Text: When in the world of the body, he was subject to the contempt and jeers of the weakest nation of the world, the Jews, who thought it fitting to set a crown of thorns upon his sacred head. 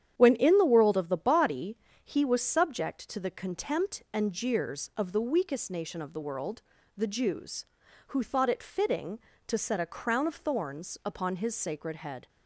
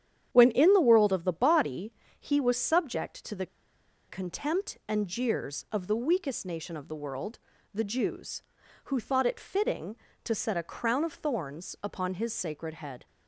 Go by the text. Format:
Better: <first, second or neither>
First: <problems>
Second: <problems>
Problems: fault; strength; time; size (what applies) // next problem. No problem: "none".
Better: first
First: starts louder than the rest; strong; until 1.1 s; 9.5 dB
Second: starts louder than the rest; strong; until 1.3 s; 9.5 dB // pauses between "the" and "contempt"; noticeable; at 3.4 s; 0.62 s long